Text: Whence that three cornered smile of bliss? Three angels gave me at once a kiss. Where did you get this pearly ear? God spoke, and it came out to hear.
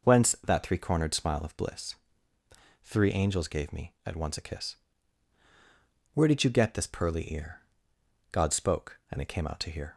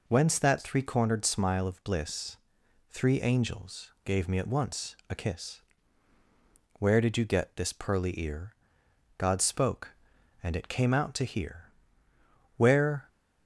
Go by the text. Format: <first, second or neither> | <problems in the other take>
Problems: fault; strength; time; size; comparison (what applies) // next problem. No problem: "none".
first | goes on to say "Where"; from 12.5 s on; 0.50 s long